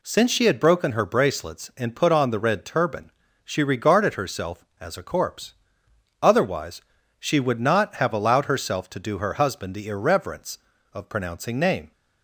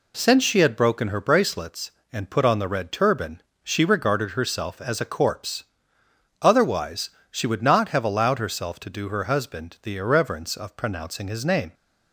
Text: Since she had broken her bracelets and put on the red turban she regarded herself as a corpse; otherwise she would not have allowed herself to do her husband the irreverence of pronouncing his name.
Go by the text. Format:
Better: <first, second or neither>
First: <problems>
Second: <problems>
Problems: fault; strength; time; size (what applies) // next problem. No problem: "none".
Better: second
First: pauses between "turban" and "she"; slight; at 3.1 s; 0.34 s long // pauses between "otherwise" and "she"; at 6.8 s; 0.38 s long // skips "his"; at 11.5 s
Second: pauses between "turban" and "she"; slight; at 3.4 s; 0.22 s long // pauses between "otherwise" and "she"; slight; at 7.0 s; 0.20 s long